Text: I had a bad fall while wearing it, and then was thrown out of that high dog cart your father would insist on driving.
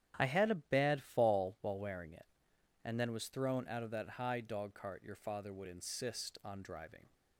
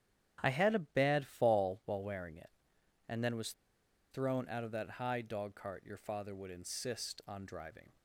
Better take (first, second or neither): first